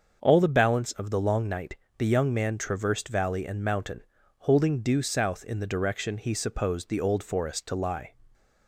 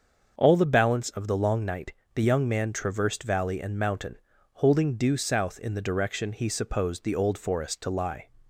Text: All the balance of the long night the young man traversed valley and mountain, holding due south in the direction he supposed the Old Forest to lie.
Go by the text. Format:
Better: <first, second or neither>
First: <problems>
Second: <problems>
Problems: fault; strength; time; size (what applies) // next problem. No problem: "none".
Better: neither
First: starts louder than the rest; until 1.2 s; 6.5 dB // pauses between "night" and "the"; slight; at 1.7 s; 0.24 s long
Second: starts louder than the rest; until 1.3 s; 6.5 dB // pauses between "night" and "the"; slight; at 1.9 s; 0.24 s long